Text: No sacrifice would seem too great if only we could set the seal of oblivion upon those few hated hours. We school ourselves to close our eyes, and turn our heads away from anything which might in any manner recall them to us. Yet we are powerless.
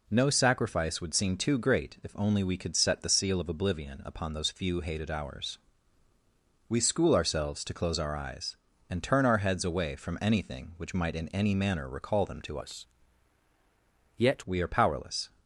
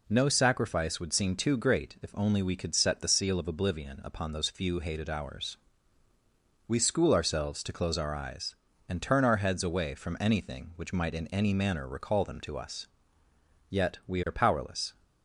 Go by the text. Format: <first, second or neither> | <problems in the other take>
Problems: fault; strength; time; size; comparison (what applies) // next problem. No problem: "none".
second | changes voice from "us" to "Yet"; from 12.6 to 14.4 s; 1.8 s long